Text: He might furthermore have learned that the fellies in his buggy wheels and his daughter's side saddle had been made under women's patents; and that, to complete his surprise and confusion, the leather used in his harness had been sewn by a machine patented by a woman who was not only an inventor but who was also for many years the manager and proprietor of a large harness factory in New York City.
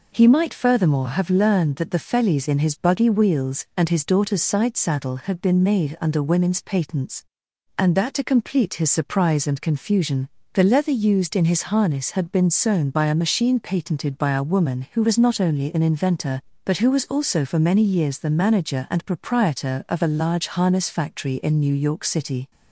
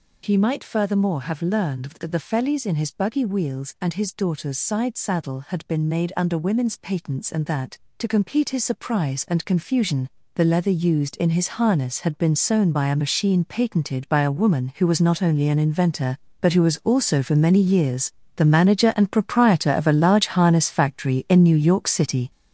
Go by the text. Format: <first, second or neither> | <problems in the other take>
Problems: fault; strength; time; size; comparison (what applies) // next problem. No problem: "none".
first | gets louder; throughout; 7 dB // pauses between "years" and "the"; slight; at 18.1 s; 0.26 s long